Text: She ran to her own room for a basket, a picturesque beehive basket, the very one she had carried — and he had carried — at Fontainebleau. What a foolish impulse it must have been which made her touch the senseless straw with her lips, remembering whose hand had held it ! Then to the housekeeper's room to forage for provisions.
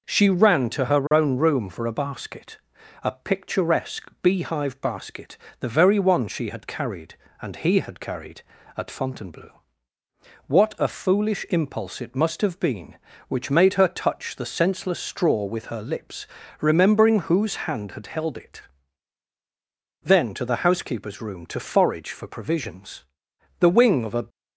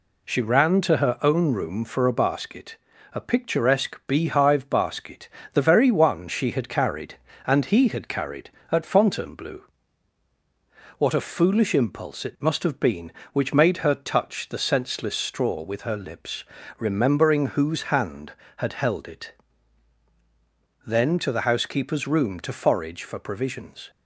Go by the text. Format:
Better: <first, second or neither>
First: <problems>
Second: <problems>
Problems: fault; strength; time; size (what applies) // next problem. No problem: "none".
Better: second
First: goes on to say "The wing of a"; noticeable; from 23.5 s on; 0.68 s long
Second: none